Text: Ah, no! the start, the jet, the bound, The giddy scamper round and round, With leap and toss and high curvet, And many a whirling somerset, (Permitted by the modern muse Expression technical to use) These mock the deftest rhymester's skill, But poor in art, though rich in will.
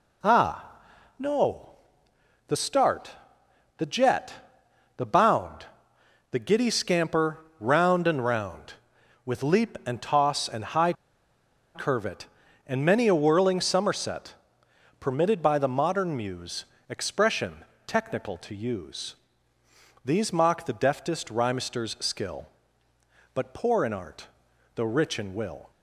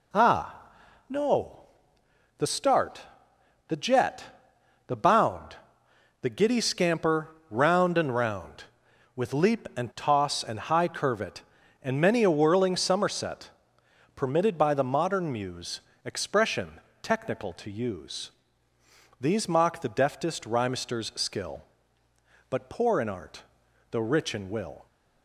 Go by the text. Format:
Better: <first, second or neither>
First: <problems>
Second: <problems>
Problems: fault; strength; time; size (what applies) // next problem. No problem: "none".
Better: second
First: pauses between "scamper" and "round"; slight; at 7.3 s; 0.20 s long // pauses between "high" and "curvet"; noticeable; at 10.9 s; 0.82 s long // pauses between "muse" and "Expression"; slight; at 16.6 s; 0.24 s long // pauses between "Expression" and "technical"; slight; at 17.6 s; 0.22 s long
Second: pauses between "scamper" and "round"; slight; at 7.2 s; 0.20 s long // pauses between "muse" and "Expression"; slight; at 15.8 s; 0.24 s long // pauses between "Expression" and "technical"; slight; at 16.7 s; 0.22 s long